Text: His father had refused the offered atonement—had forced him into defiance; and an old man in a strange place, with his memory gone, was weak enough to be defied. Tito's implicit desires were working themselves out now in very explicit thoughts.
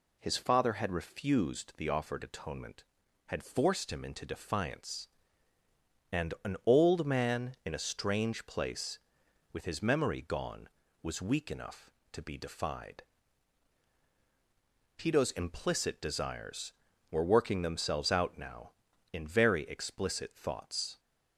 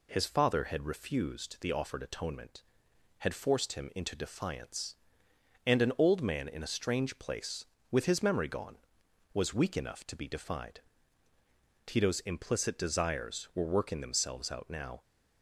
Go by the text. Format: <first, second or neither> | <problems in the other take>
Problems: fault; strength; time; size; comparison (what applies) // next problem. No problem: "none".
first | stops before "in very explicit thoughts"; at 15.0 s